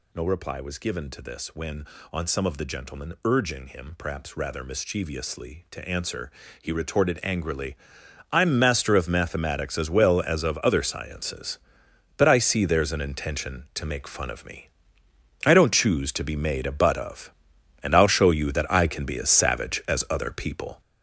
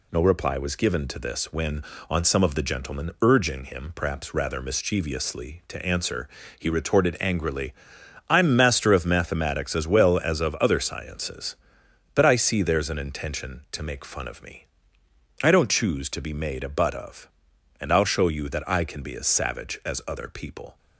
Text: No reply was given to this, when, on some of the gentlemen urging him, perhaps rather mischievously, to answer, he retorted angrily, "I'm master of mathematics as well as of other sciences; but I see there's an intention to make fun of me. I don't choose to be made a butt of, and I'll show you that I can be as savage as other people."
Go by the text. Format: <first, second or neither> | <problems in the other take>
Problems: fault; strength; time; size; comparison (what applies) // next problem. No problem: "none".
second | gets louder; throughout; 7 dB